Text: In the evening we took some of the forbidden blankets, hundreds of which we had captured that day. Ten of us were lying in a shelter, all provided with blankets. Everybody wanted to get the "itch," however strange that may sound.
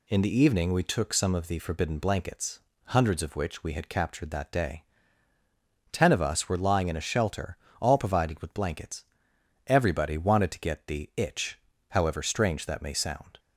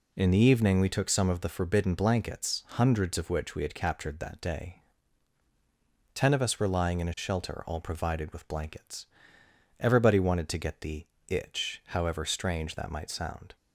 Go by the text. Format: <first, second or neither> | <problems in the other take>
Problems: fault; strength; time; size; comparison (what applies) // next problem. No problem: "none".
first | pauses between "the" and "itch"; slight; at 11.0 s; 0.22 s long // says "might" for "may"; at 12.9 s